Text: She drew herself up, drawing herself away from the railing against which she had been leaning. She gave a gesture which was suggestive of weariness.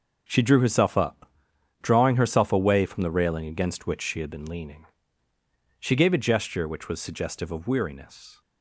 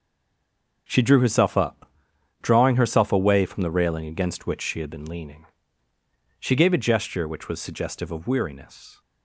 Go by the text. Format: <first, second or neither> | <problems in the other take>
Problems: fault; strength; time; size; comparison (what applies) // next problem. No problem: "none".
first | stays silent before the first word; slight; until 0.8 s; 0.8 s long